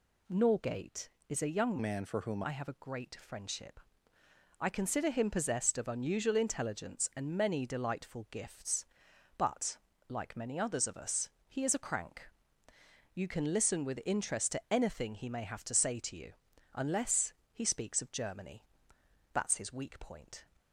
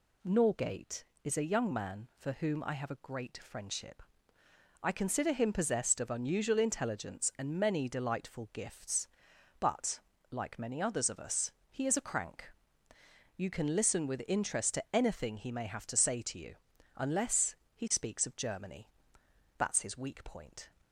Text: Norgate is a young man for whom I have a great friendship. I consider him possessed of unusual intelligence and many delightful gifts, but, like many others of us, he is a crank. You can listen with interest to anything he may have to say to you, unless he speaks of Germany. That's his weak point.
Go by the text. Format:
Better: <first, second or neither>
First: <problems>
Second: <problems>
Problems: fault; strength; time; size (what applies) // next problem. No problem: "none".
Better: second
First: changes voice from "man" to "whom"; from 1.8 to 2.4 s; 0.6 s long // pauses between "unless" and "he"; slight; at 17.3 s; 0.20 s long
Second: pauses between "unless" and "he"; slight; at 17.5 s; 0.20 s long